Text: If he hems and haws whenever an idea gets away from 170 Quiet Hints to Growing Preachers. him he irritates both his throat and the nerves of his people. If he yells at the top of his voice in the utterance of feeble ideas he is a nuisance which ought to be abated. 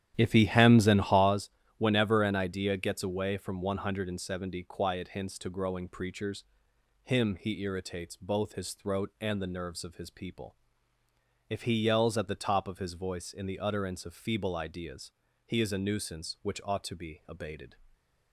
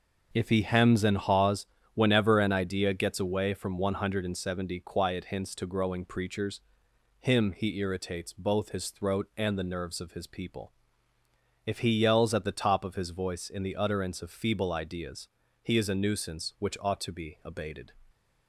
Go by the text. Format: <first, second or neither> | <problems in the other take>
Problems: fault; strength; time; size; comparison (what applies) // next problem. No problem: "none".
second | starts louder than the rest; strong; until 1.4 s; 11 dB // pauses between "haws" and "whenever"; slight; at 1.4 s; 0.28 s long; slight in the second // pauses between "ideas" and "he"; slight; at 15.1 s; 0.34 s long; slight in the second